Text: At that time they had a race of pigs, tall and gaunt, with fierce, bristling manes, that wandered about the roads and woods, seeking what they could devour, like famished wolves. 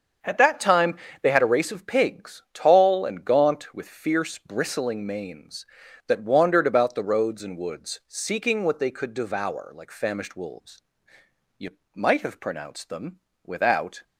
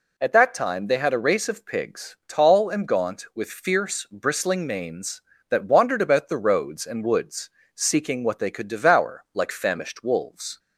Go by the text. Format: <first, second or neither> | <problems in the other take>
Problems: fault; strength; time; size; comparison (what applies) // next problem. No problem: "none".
second | starts louder than the rest; until 1.4 s; 7 dB // pauses between "time" and "they"; slight; at 0.9 s; 0.26 s long // goes on to say "You might have pronounced them without"; strong; from 11.5 s on; 2.4 s long